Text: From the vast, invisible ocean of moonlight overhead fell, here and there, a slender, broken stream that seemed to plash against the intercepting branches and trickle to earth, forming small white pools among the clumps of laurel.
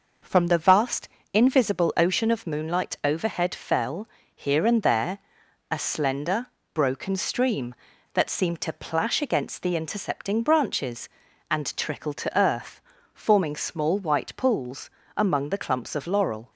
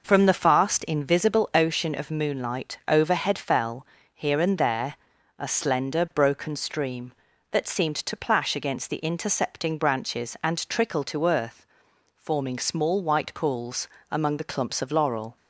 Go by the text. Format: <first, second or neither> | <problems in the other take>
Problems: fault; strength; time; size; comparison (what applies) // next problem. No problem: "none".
first | says "fast" for "vast"; at 0.3 s // pauses between "pools" and "among"; slight; at 13.8 s; 0.20 s long; slight in the first